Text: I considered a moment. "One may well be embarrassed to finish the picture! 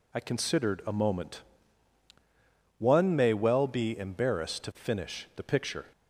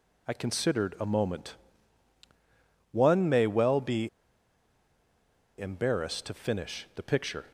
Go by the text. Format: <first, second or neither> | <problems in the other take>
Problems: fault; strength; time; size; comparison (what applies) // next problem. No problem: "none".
first | pauses between "be" and "embarrassed"; strong; at 4.0 s; 1.5 s long